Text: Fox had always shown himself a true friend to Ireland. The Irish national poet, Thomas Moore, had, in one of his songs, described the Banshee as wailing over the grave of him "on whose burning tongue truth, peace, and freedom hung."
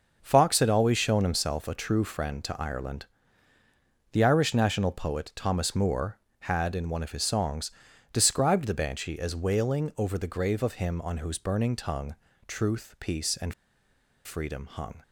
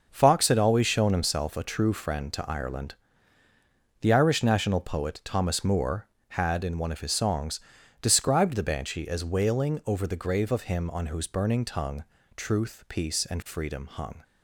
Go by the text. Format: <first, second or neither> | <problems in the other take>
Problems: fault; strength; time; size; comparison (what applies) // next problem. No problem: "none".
second | starts louder than the rest; noticeable; until 1.2 s; 6 dB; noticeable in the second // pauses between "tongue" and "truth"; slight; at 12.1 s; 0.32 s long; slight in the second // pauses between "and" and "freedom"; noticeable; at 13.5 s; 0.72 s long